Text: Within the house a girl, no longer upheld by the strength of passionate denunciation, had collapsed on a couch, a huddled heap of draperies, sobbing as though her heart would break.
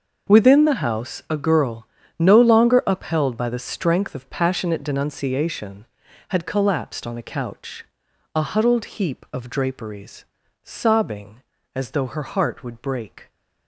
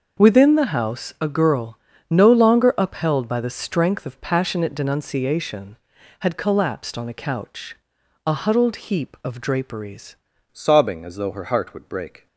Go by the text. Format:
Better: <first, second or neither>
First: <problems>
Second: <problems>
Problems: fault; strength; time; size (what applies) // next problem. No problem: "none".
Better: first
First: none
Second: starts louder than the rest; noticeable; until 1.2 s; 6 dB // changes voice at "sobbing"; from 10.5 s on; 1.7 s long